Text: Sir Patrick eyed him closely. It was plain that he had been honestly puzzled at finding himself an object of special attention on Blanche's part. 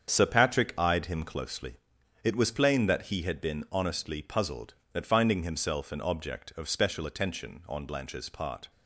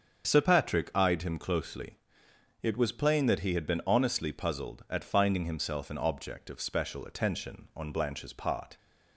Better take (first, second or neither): neither